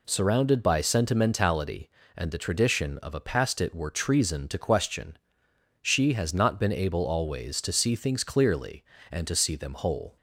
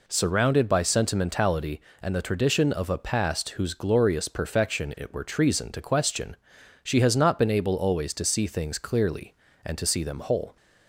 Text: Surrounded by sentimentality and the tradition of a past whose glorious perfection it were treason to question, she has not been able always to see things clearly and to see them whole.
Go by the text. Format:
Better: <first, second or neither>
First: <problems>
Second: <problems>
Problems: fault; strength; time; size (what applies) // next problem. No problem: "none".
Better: second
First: skips "whose glorious perfection"; at 3.5 s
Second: none